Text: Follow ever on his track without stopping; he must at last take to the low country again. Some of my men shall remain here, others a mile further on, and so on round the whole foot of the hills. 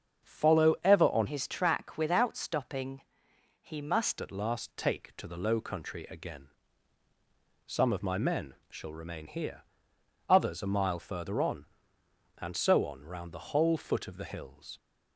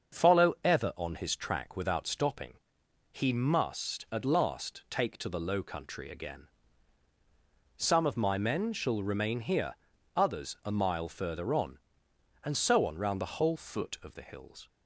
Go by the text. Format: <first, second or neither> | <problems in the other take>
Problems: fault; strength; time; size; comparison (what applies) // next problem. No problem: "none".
second | starts louder than the rest; until 1.3 s; 7 dB; also in the second // changes voice from "his" to "must"; from 1.2 to 4.1 s; 2.9 s long // pauses between "men" and "shall"; slight; at 8.5 s; 0.16 s long